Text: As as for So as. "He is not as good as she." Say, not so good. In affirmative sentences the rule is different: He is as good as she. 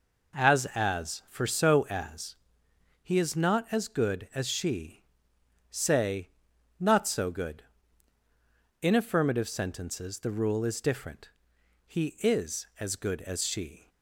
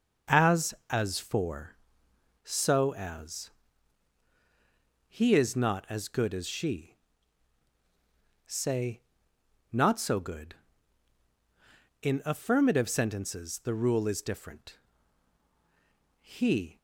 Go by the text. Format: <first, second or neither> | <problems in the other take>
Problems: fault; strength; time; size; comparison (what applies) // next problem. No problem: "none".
first | starts louder than the rest; until 1.4 s; 6.5 dB // stops before "is as good as she"; at 16.7 s